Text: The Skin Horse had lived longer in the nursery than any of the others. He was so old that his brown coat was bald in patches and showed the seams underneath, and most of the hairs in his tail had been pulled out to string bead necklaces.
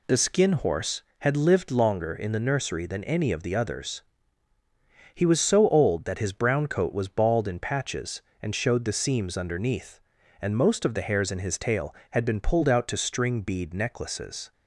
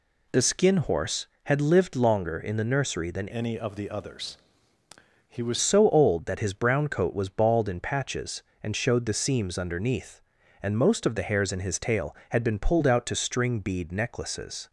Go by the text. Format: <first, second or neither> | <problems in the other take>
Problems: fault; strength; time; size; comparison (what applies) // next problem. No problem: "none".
first | changes voice from "any" to "was"; from 3.3 to 5.5 s; 2.2 s long